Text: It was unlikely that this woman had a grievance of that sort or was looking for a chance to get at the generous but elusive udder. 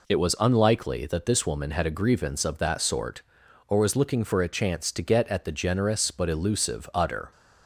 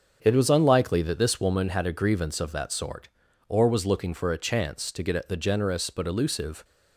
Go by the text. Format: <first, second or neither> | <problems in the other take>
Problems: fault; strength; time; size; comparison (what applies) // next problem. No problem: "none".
first | starts louder than the rest; strong; until 1.2 s; 7 dB // stops before "udder"; at 6.6 s